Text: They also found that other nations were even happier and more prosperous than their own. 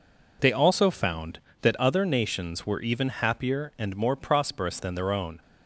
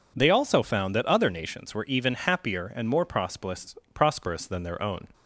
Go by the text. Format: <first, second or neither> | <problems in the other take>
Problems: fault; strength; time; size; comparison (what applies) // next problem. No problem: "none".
first | says "prosperous" twice; at 3.9 s